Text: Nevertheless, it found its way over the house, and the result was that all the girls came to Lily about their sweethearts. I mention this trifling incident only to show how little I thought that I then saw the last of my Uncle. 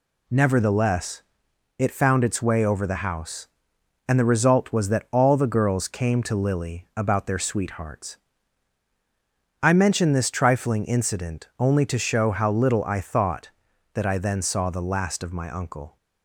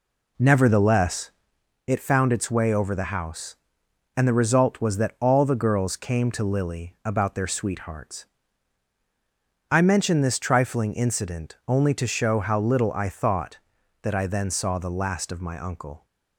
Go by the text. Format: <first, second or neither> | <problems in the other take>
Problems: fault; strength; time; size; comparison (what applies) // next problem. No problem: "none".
first | starts louder than the rest; slight; until 1.6 s; 3 dB